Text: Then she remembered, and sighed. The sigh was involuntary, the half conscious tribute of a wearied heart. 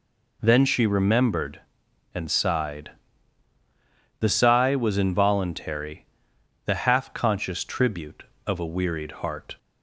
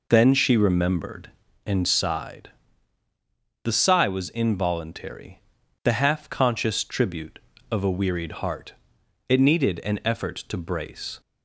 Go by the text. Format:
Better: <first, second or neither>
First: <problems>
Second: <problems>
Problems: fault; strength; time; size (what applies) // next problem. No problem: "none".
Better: first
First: none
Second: goes on to say "It needed an effort to brace"; strong; from 9.3 s on; 1.9 s long